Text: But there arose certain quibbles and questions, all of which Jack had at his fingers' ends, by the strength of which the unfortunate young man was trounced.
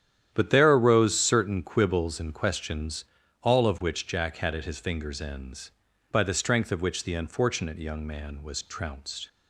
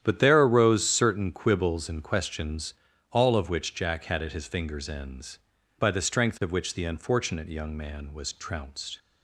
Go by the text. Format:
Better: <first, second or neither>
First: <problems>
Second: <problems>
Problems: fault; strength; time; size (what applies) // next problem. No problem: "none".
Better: neither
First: starts louder than the rest; strong; until 1.3 s; 10 dB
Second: starts louder than the rest; strong; until 1.0 s; 10 dB